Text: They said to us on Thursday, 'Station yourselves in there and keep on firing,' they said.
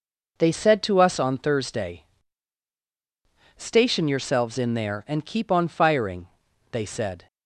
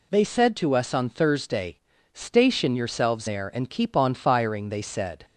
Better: first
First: none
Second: skips "in"; at 3.2 s

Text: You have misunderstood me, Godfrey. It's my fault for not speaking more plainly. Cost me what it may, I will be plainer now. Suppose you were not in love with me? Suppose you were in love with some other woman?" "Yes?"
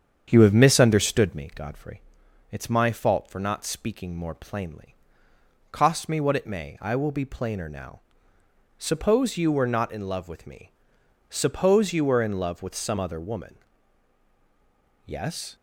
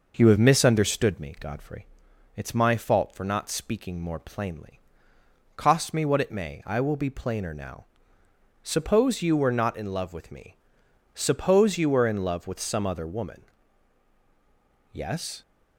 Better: second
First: starts louder than the rest; strong; until 1.5 s; 8 dB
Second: none

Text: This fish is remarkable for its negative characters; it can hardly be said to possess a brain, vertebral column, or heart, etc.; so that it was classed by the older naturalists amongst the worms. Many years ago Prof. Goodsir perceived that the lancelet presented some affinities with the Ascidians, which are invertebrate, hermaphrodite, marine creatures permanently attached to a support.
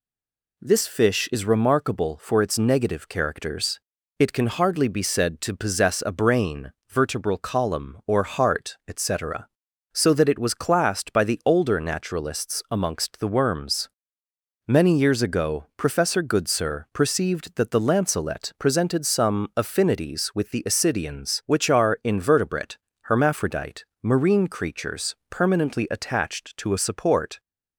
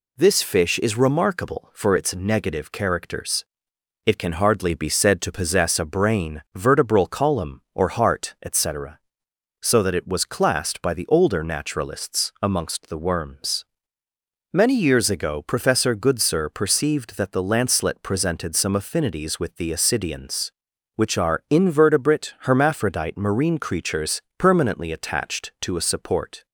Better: second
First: stays silent before the first word; slight; until 0.5 s; 0.5 s long // pauses between "creatures" and "permanently"; slight; at 25.1 s; 0.16 s long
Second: pauses between "creatures" and "permanently"; slight; at 24.2 s; 0.18 s long

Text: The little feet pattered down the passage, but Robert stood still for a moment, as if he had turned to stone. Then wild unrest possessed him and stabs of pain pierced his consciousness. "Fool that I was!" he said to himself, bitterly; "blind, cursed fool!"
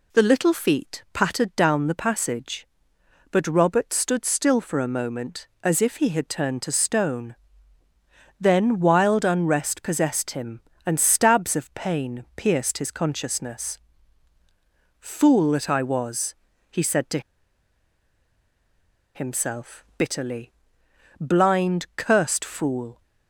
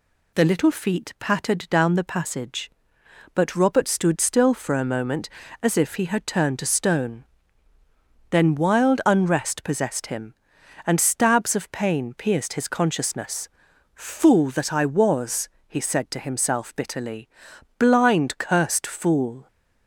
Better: second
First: pauses between "to" and "himself"; strong; at 17.2 s; 1.9 s long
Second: none

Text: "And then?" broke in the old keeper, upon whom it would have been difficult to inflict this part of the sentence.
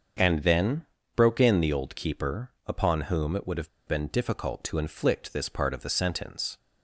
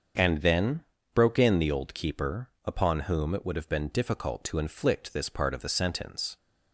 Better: second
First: starts louder than the rest; until 1.5 s; 7 dB // pauses between "have" and "been"; slight; at 3.6 s; 0.18 s long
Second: starts louder than the rest; until 1.4 s; 7 dB

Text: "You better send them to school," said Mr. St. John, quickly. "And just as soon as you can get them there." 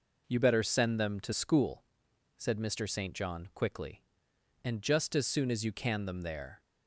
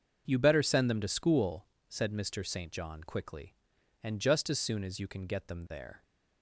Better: second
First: skips "get"; at 6.0 s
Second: none

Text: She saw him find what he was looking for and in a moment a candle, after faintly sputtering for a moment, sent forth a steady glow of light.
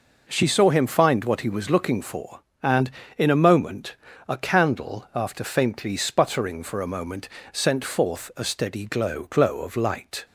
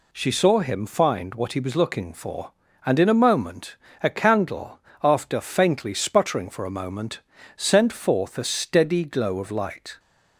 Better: second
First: pauses between "moment" and "a"; slight; at 3.9 s; 0.32 s long // says "glow" twice; at 9.2 s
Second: pauses between "moment" and "a"; slight; at 3.7 s; 0.26 s long

